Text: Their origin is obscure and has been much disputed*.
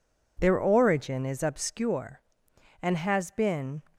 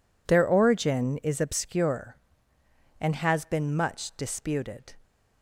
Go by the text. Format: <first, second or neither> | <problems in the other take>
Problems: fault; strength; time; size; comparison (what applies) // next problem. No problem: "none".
second | stops before "much disputed"; at 3.9 s